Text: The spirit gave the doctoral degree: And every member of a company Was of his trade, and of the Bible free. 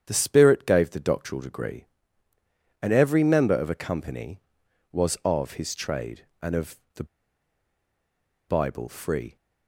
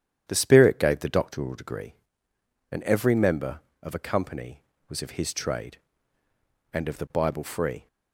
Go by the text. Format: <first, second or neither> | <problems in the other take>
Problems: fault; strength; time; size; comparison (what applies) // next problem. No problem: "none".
second | starts louder than the rest; strong; until 1.0 s; 8.5 dB; strong in the second // pauses between "of" and "the"; slight; at 6.7 s; 0.18 s long // pauses between "the" and "Bible"; strong; at 7.0 s; 1.4 s long